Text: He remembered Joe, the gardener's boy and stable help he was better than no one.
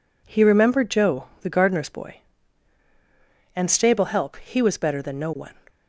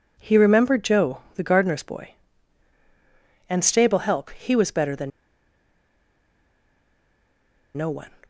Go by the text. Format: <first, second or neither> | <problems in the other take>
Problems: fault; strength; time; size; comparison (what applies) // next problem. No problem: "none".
first | pauses between "than" and "no"; strong; at 5.1 s; 2.6 s long